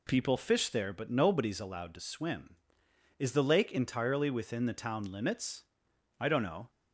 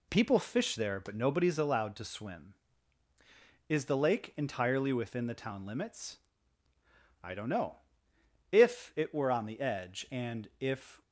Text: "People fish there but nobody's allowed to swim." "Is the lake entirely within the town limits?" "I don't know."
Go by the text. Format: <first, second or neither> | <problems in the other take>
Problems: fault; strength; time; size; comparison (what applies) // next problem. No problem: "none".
first | goes on to say "If it were on the edge and if"; strong; from 8.5 s on; 2.5 s long